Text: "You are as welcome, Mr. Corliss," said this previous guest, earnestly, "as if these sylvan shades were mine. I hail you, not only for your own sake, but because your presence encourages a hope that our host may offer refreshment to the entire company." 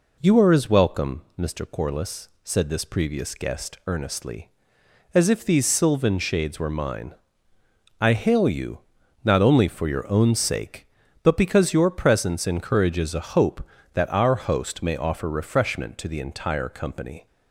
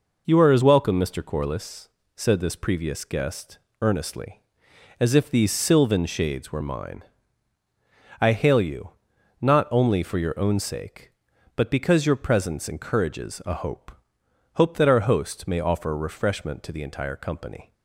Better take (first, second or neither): first